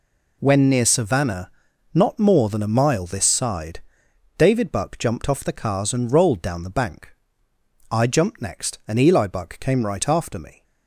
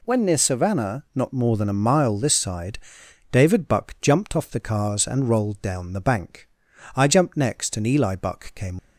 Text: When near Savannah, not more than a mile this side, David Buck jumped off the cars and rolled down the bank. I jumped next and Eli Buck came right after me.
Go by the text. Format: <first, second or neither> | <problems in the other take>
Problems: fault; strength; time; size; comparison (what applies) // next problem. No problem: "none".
first | stops before "right after me"; at 8.7 s